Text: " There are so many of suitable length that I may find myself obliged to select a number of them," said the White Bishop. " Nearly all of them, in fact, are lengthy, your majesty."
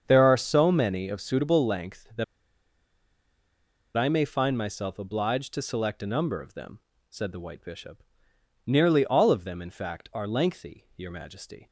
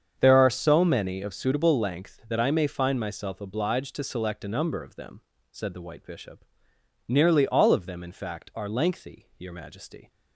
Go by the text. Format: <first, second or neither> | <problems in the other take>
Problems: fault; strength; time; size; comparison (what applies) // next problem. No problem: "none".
second | starts louder than the rest; strong; until 1.0 s; 7.5 dB; strong in the second // pauses between "that" and "I"; strong; at 2.2 s; 1.7 s long